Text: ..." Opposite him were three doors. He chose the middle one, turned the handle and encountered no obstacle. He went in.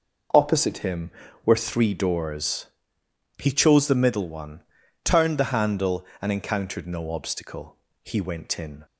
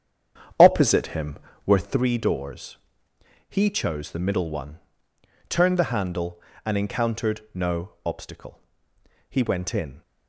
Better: first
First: none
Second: starts louder than the rest; strong; until 2.0 s; 8.5 dB

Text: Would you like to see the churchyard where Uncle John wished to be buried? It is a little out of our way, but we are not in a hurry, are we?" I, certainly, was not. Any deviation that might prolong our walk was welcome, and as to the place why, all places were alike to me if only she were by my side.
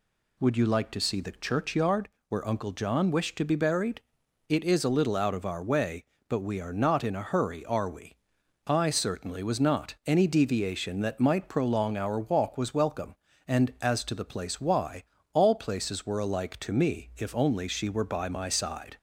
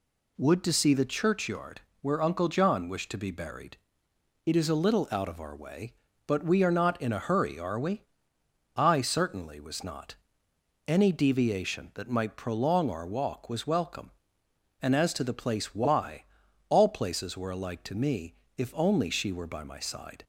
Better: first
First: pauses between "churchyard" and "where"; slight; at 2.0 s; 0.20 s long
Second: skips "you like"; at 0.6 s // pauses between "churchyard" and "where"; slight; at 1.8 s; 0.20 s long // pauses between "me" and "if"; slight; at 18.3 s; 0.24 s long

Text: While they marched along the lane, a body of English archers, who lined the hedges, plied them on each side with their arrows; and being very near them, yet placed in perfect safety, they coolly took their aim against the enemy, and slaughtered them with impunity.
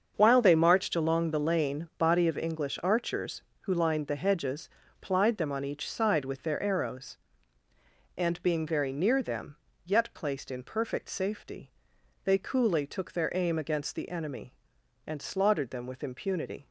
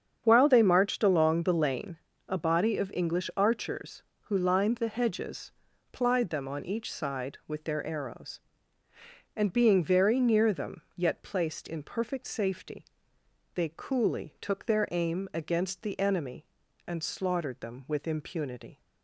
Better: second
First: starts louder than the rest; until 1.1 s; 7 dB // skips "a"; at 1.9 s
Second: starts louder than the rest; strong; until 1.2 s; 7.5 dB

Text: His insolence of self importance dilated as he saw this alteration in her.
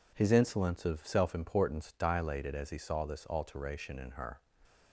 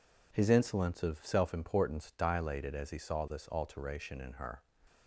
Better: neither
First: none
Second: none

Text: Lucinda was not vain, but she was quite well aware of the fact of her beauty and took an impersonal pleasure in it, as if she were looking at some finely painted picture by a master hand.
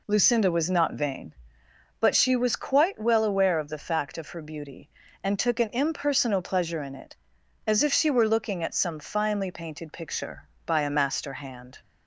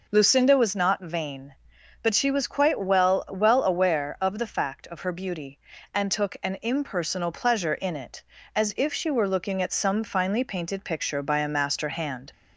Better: first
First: none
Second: says "well" twice; at 3.2 s

